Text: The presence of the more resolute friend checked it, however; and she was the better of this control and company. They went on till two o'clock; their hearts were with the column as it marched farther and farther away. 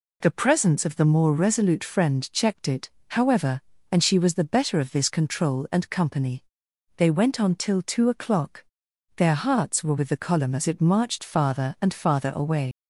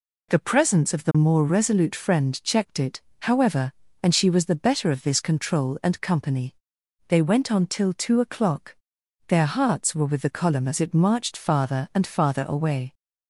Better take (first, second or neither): second